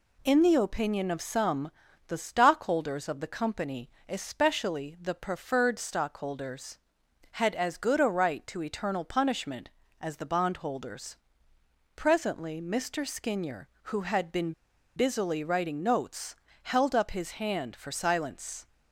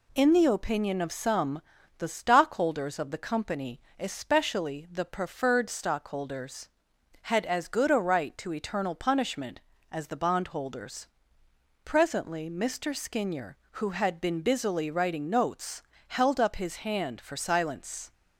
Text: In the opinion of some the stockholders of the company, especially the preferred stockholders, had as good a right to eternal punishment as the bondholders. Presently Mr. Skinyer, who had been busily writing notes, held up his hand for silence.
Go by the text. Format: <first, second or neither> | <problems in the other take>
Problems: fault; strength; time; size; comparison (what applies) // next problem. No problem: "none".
second | pauses between "some" and "the"; slight; at 1.7 s; 0.36 s long; slight in the second // pauses between "been" and "busily"; at 14.5 s; 0.44 s long